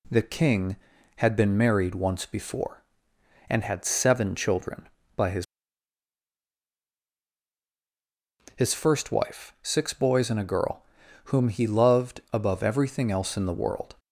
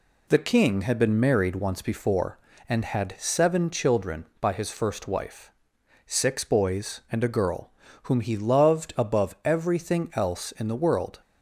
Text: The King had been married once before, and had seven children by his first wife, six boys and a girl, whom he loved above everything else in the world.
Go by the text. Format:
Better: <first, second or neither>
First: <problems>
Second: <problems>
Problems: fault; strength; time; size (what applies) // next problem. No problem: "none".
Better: second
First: says "his" twice; at 8.5 s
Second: none